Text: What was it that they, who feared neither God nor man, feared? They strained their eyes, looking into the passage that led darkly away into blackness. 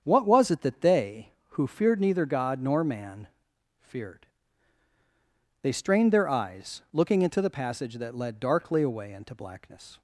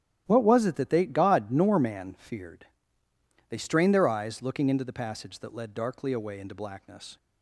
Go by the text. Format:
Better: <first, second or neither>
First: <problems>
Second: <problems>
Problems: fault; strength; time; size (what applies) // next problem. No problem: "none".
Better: first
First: starts louder than the rest; strong; until 1.0 s; 7.5 dB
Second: starts louder than the rest; strong; until 1.2 s; 11.5 dB // skips "who feared neither"; at 1.0 s